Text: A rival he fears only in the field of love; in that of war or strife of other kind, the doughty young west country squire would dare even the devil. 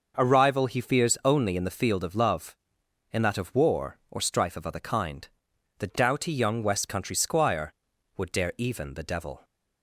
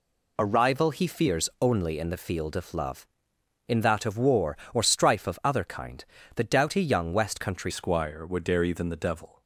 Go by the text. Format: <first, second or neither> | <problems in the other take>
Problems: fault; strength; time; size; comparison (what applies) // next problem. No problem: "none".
first | changes voice at "squire"; from 7.6 s on; 1.8 s long